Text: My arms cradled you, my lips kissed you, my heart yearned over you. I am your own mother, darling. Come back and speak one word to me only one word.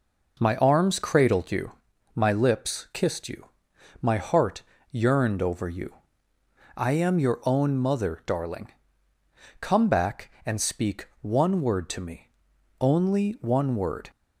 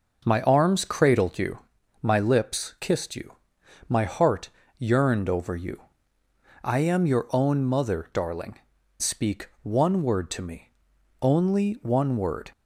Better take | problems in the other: first | pauses between "heart" and "yearned"; slight; at 4.4 s; 0.30 s long; slight in the first // skips "Come back and"; at 8.7 s // pauses between "me" and "only"; noticeable; at 10.6 s; 0.54 s long; noticeable in the first

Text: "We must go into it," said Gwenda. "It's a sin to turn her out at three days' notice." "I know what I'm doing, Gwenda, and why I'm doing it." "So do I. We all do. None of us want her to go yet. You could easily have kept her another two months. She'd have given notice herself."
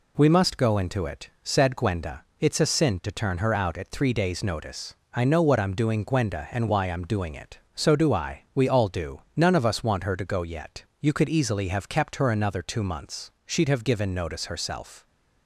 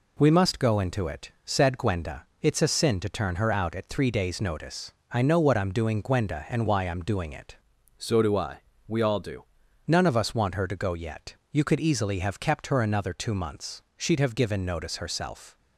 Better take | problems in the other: first | changes voice from "So" to "do"; from 7.9 to 9.4 s; 1.5 s long

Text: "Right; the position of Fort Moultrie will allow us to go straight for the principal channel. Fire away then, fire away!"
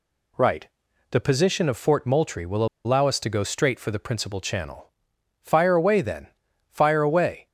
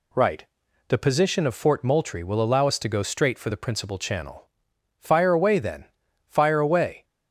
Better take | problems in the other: second | pauses between "will" and "allow"; slight; at 2.6 s; 0.19 s long

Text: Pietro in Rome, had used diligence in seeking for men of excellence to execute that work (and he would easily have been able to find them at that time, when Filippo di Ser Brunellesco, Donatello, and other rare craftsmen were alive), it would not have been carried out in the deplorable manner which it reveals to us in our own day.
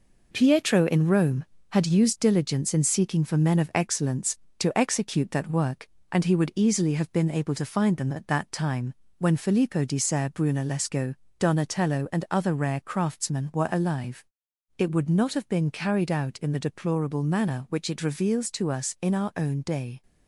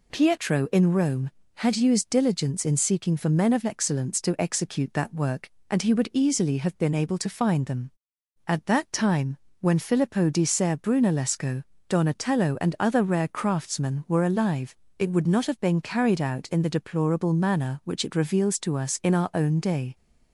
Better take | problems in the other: second | gets quieter; noticeable; throughout; 5 dB

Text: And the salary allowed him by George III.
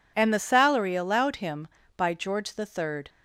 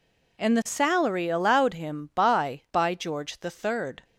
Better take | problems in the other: first | says "by" twice; at 2.6 s

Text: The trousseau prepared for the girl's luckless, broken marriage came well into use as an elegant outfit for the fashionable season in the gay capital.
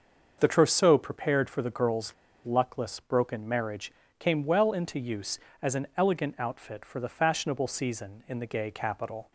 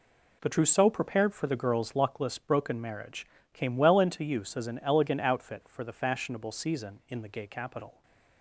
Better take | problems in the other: second | starts louder than the rest; until 1.4 s; 6.5 dB // pauses between "girl's" and "luckless"; slight; at 2.1 s; 0.31 s long // pauses between "marriage" and "came"; slight; at 3.9 s; 0.28 s long; slight in the second

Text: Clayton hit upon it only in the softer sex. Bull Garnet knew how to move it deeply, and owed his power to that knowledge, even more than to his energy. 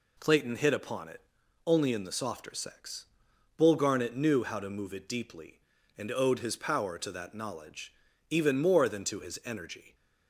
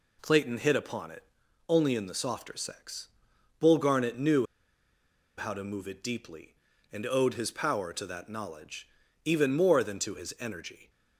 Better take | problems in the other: first | pauses between "it" and "only"; at 1.2 s; 0.44 s long; also in the first // pauses between "knew" and "how"; noticeable; at 4.4 s; 0.91 s long

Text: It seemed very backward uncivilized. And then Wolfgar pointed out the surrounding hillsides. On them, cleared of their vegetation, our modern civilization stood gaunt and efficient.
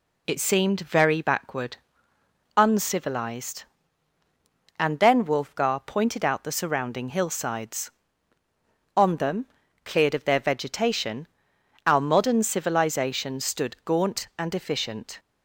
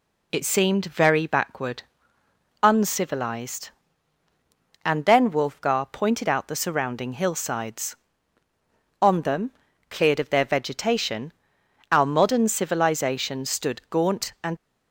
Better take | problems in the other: first | pauses between "backward" and "uncivilized"; noticeable; at 1.8 s; 0.80 s long; noticeable in the first // stops before "efficient"; at 14.5 s

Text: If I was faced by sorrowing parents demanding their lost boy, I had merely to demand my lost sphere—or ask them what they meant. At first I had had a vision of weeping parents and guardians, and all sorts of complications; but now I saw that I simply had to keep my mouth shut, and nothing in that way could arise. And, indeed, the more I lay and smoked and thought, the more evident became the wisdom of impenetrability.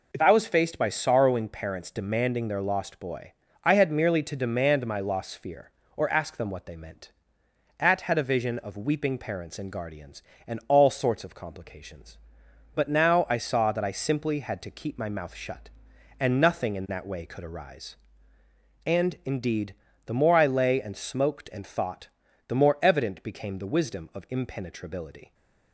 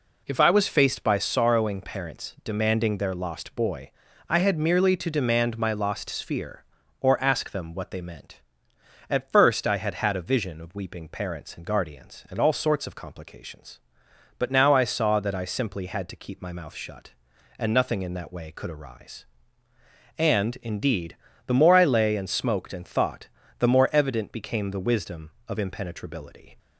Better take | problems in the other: second | skips "first I had"; at 8.0 s

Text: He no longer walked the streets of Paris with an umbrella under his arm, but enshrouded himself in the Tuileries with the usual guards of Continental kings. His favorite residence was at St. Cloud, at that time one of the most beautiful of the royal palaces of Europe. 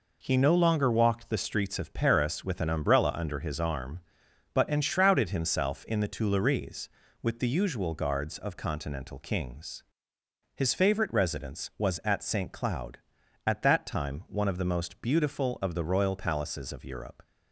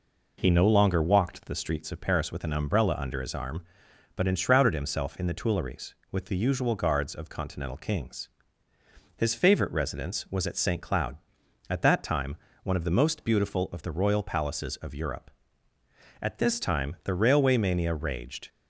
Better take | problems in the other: first | pauses between "time" and "one"; slight; at 12.3 s; 0.26 s long // goes on to say "At this time the railway mania raged"; strong; from 16.2 s on; 2.2 s long

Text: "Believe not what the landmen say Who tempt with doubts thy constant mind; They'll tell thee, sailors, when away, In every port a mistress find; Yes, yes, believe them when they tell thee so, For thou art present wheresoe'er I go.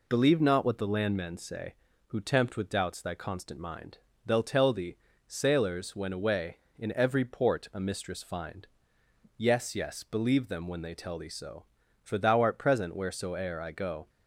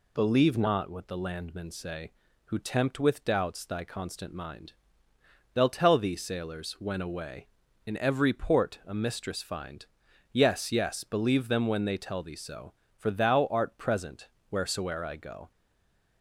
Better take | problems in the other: first | pauses between "present" and "wheresoe'er"; slight; at 14.2 s; 0.22 s long // stays silent after the last word; slight; from 15.5 s on; 0.7 s long

